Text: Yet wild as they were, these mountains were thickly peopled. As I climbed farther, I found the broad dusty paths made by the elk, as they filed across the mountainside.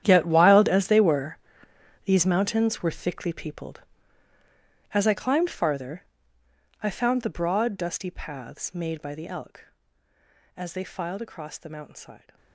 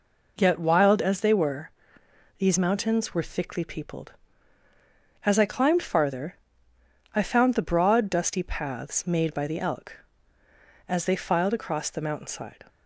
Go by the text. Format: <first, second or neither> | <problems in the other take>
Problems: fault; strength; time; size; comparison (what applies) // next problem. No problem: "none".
second | gets quieter; strong; throughout; 17 dB